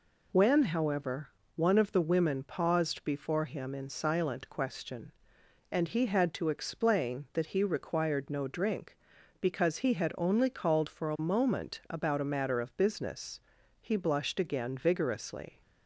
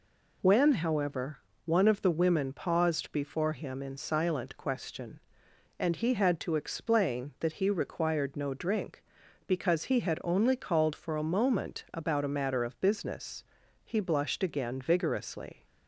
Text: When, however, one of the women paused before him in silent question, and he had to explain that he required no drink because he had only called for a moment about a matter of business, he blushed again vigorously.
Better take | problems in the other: neither | none

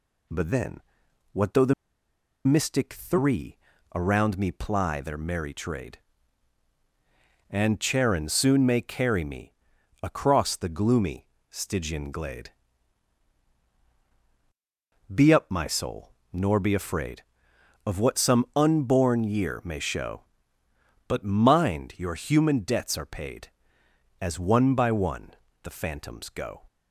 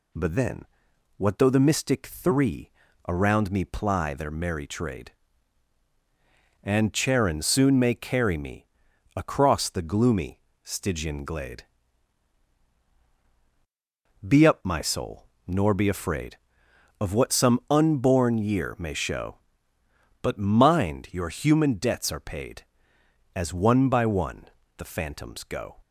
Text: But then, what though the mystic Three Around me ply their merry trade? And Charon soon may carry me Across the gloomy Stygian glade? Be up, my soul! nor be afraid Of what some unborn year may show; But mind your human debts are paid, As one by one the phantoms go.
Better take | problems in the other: second | pauses between "the" and "mystic"; noticeable; at 1.7 s; 0.73 s long // pauses between "Three" and "Around"; at 3.5 s; 0.38 s long; also in the second // pauses between "me" and "Across"; noticeable; at 9.5 s; 0.48 s long; noticeable in the second // pauses between "gloomy" and "Stygian"; slight; at 11.2 s; 0.24 s long; slight in the second // pauses between "one" and "the"; slight; at 25.3 s; 0.28 s long; slight in the second

